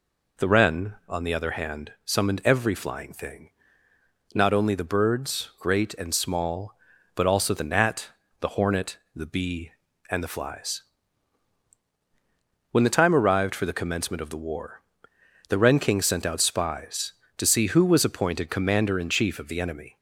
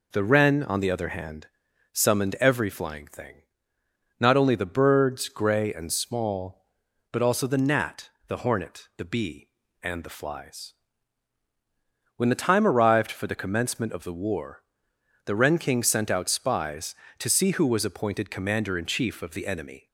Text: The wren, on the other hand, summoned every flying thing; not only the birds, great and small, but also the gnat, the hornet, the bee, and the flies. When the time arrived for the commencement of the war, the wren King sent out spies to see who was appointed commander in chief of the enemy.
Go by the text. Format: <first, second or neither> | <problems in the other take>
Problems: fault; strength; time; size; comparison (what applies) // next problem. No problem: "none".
first | says "grey" for "great"; at 5.2 s